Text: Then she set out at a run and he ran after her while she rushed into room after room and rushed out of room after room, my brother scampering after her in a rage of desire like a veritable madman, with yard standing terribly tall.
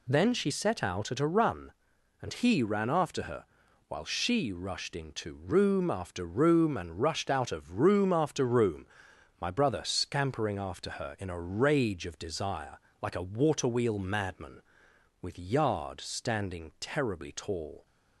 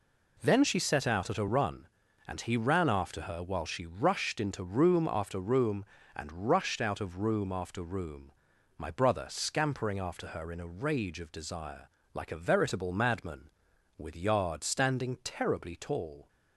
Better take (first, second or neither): second